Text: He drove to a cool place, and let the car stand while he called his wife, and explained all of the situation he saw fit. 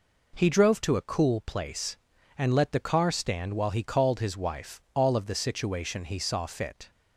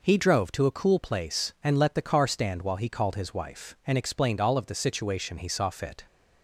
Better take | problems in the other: second | skips "and explained"; at 4.8 s

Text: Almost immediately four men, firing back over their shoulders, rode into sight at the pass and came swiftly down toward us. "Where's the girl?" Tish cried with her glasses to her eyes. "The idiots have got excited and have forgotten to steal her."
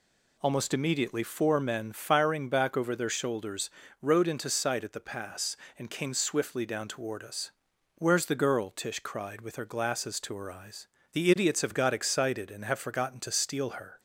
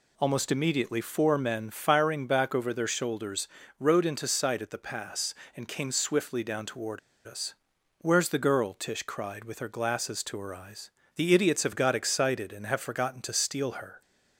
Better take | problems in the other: first | pauses between "toward" and "us"; slight; at 6.9 s; 0.27 s long

